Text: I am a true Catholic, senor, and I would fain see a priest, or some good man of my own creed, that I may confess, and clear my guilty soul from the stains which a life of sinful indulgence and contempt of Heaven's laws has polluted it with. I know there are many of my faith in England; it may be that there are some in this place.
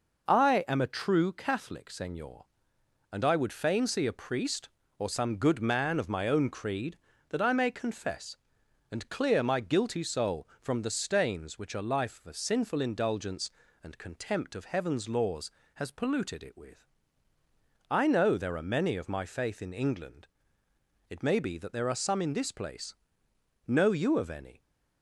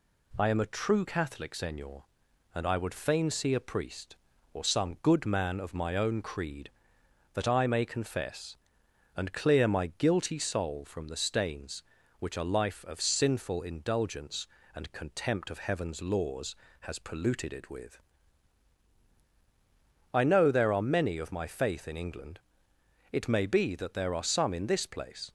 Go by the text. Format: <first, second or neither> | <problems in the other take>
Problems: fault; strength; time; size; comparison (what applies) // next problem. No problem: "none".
second | goes on to say "Know you of any"; noticeable; from 23.6 s on; 0.94 s long